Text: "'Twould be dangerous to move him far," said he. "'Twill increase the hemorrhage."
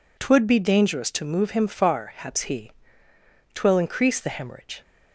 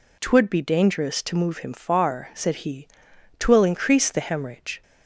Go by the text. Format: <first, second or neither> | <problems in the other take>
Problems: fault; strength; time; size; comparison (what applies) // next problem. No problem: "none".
second | says "haps" for "said"; at 2.0 s